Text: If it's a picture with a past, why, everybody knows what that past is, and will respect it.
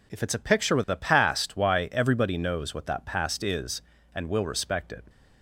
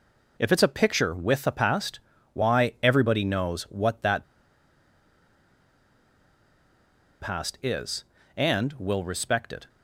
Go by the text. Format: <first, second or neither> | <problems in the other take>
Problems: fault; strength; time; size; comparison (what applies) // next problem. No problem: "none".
first | pauses between "that" and "past"; strong; at 4.2 s; 2.9 s long